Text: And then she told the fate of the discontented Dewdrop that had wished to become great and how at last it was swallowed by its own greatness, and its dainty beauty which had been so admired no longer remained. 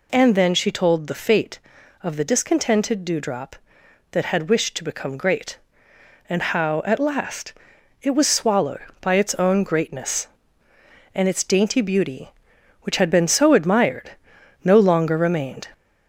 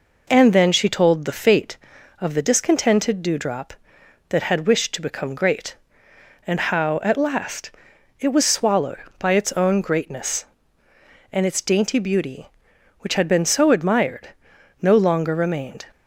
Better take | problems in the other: second | gets louder; slight; throughout; 2.5 dB // pauses between "last" and "it"; noticeable; at 7.5 s; 0.50 s long; noticeable in the second // pauses between "admired" and "no"; noticeable; at 14.1 s; 0.54 s long; noticeable in the second

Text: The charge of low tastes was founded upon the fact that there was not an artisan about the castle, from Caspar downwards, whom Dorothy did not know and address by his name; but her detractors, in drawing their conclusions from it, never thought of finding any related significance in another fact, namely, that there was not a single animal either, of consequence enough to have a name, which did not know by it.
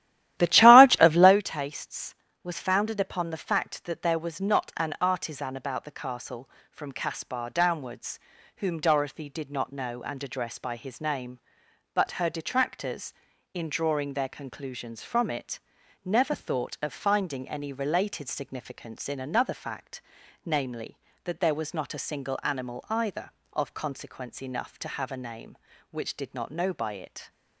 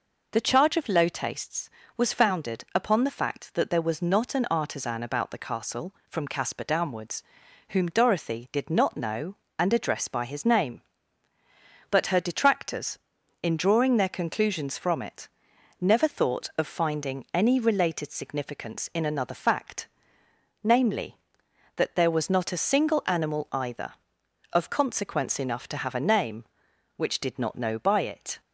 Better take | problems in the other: second | starts louder than the rest; strong; until 1.4 s; 13.5 dB

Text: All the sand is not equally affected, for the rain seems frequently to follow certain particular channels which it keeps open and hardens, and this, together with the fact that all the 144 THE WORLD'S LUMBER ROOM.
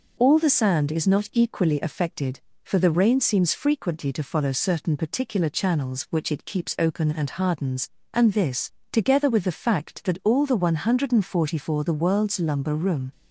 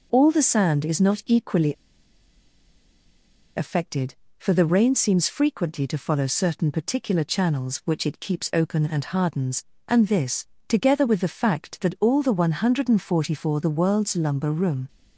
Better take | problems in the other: first | pauses between "equally" and "affected"; strong; at 1.7 s; 1.8 s long

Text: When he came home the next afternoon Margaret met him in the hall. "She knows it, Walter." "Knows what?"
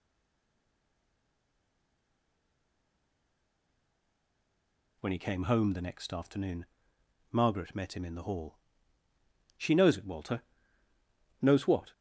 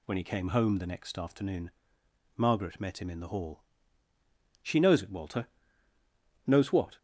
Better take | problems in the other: second | stays silent before the first word; strong; until 5.0 s; 5.0 s long // pauses between "afternoon" and "Margaret"; noticeable; at 6.6 s; 0.64 s long; noticeable in the second

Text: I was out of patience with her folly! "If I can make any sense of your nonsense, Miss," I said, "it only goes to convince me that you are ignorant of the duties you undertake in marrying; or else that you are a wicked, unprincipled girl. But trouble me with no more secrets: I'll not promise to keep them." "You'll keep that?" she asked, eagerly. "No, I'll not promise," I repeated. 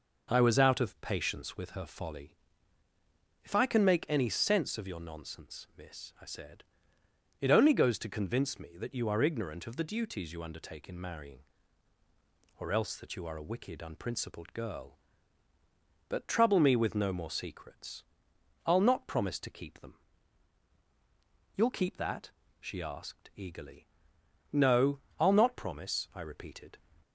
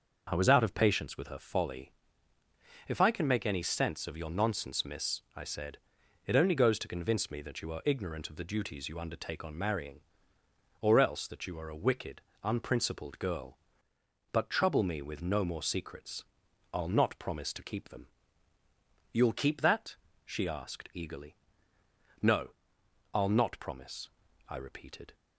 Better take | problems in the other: first | starts louder than the rest; until 1.3 s; 6 dB // says "on" for "in"; at 9.4 s

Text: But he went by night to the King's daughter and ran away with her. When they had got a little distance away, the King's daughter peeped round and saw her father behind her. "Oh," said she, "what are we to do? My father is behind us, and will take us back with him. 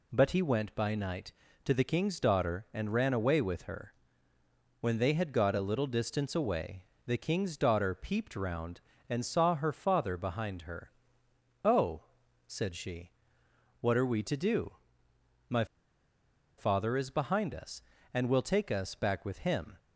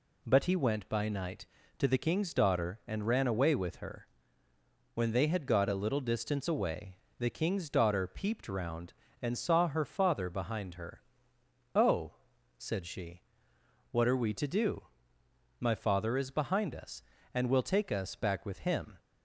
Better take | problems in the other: second | pauses between "My" and "father"; noticeable; at 15.6 s; 0.93 s long

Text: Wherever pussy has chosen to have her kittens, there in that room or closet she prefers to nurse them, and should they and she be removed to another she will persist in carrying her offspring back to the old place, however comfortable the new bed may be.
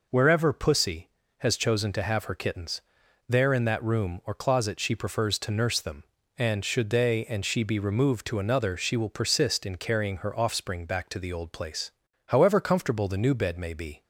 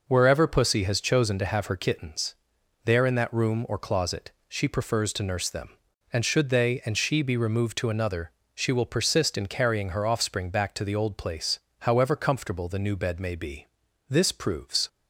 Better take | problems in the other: first | pauses between "closet" and "she"; slight; at 4.3 s; 0.16 s long // pauses between "another" and "she"; slight; at 8.3 s; 0.22 s long // goes on to say "This proves"; noticeable; from 14.0 s on; 0.80 s long

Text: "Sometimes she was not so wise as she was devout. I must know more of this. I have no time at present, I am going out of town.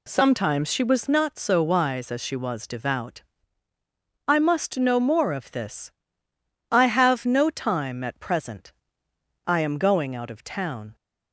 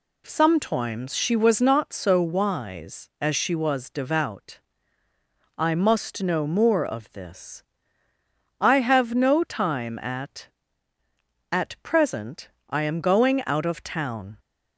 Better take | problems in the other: first | says "at" twice; at 11.5 s

